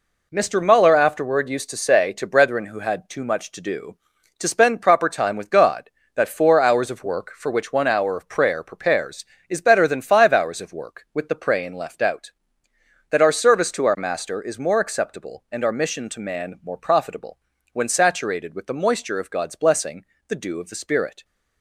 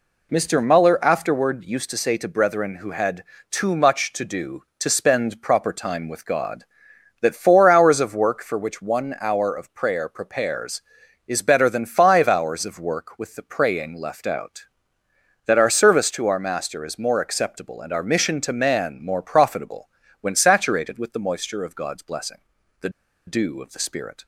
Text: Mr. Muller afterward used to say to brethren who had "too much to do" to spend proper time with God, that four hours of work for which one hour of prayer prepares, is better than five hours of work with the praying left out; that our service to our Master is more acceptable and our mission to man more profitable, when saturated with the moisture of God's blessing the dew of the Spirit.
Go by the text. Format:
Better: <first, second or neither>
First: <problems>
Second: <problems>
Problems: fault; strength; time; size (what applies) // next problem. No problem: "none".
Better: first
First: pauses between "blessing" and "the"; slight; at 20.0 s; 0.24 s long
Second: pauses between "had" and "too"; slight; at 3.2 s; 0.26 s long // pauses between "blessing" and "the"; at 22.3 s; 0.44 s long // pauses between "the" and "dew"; at 22.8 s; 0.37 s long